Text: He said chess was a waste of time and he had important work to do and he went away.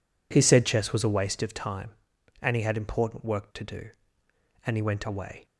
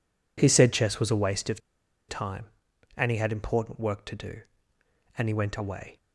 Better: first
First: none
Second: pauses between "of" and "time"; noticeable; at 1.5 s; 0.49 s long

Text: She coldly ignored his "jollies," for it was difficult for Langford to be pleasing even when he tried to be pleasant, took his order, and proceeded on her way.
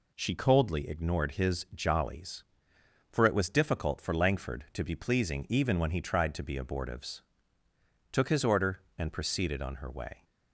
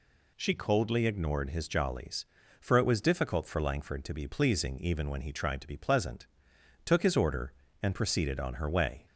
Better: second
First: says "abortives" for "pleasant"; at 6.5 s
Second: none

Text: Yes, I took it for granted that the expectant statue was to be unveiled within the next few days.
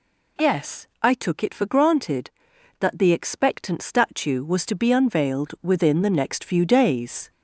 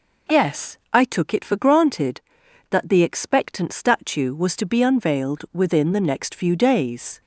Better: second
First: gets louder; slight; throughout; 3 dB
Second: none

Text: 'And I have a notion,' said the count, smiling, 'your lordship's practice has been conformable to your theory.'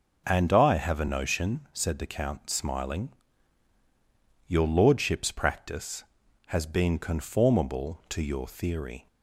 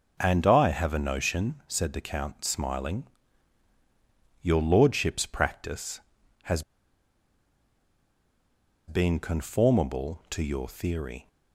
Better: first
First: none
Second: pauses between "has" and "been"; strong; at 6.6 s; 2.2 s long

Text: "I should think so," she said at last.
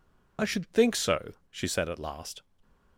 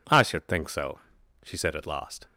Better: second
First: loses the start of "I"; at 0.3 s; 35 ms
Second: none

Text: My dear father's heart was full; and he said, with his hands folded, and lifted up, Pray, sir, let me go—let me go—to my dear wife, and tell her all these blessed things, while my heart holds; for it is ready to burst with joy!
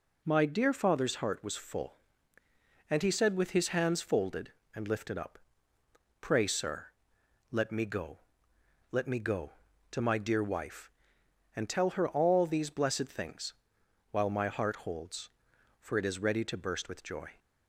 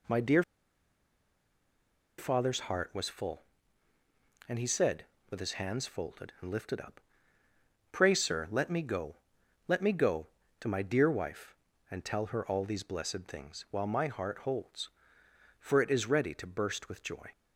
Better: first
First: none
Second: pauses between "dear" and "father's"; strong; at 0.4 s; 1.7 s long

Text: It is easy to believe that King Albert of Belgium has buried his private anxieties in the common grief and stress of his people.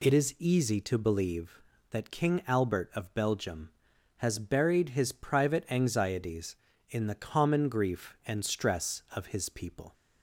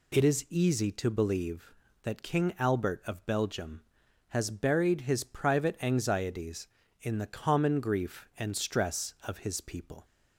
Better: neither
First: none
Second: none

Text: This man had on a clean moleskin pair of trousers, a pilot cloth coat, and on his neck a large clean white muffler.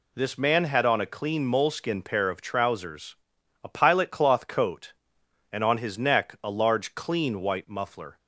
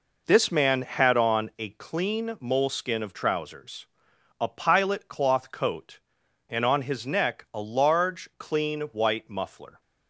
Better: first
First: none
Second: skips "pair"; at 3.0 s

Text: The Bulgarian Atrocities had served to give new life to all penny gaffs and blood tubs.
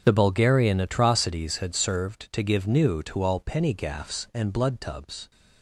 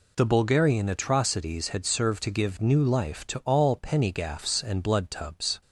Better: second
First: starts louder than the rest; strong; until 1.0 s; 7.5 dB // skips "life"; at 3.0 s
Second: none

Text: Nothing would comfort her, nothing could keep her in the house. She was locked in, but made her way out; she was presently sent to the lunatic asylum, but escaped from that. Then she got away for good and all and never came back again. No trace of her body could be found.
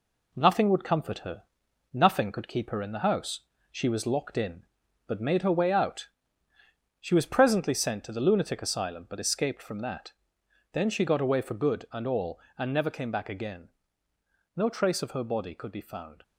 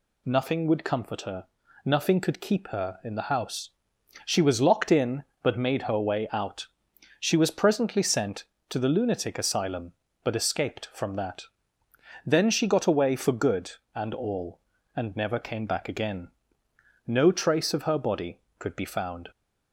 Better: second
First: gets quieter; noticeable; throughout; 4.5 dB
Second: none

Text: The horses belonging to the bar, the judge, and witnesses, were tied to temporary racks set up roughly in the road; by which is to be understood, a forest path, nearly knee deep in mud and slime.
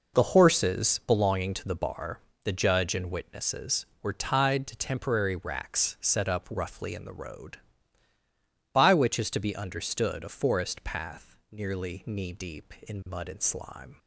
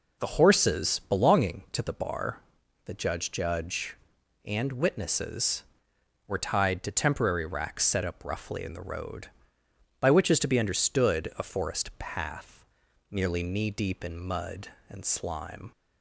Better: first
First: none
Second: says "judge" twice; at 3.3 s

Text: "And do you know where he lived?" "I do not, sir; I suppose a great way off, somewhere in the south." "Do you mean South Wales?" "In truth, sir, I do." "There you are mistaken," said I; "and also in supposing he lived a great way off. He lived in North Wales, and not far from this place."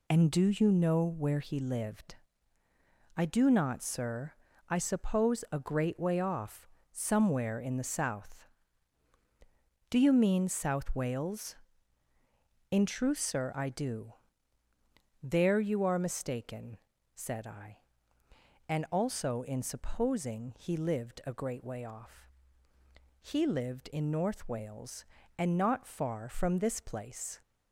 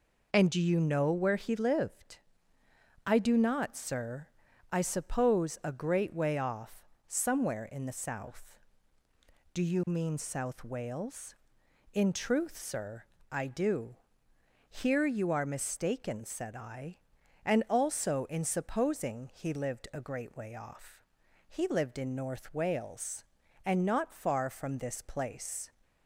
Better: first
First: none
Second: says "Here" for "There"; at 14.6 s

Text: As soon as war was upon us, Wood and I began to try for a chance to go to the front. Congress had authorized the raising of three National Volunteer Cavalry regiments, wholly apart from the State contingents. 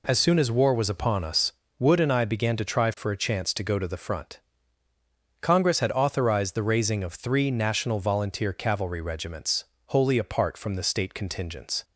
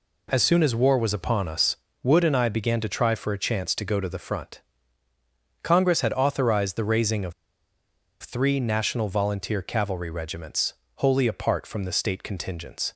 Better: first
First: none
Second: pauses between "of" and "three"; noticeable; at 7.3 s; 0.88 s long

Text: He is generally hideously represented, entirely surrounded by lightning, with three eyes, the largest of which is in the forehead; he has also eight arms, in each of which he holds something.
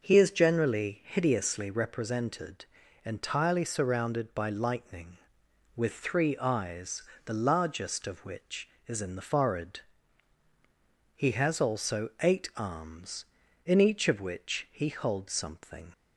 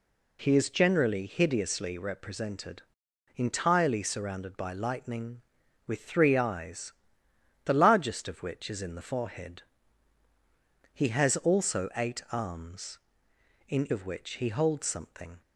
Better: first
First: none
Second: skips "each"; at 13.8 s

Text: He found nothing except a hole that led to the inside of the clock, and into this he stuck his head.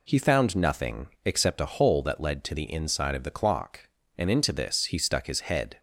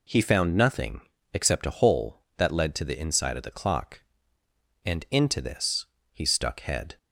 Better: first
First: pauses between "nothing" and "except"; slight; at 1.0 s; 0.16 s long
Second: pauses between "nothing" and "except"; slight; at 1.0 s; 0.32 s long // pauses between "this" and "he"; slight; at 5.8 s; 0.26 s long // skips "his"; at 6.5 s

